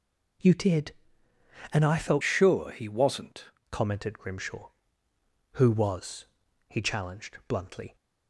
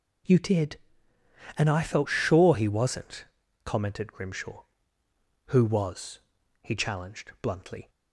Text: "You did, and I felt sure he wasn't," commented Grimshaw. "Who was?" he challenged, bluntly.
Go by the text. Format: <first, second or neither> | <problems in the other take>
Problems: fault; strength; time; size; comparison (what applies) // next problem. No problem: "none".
second | changes voice from "sure" to "wasn't"; from 2.2 to 3.5 s; 1.3 s long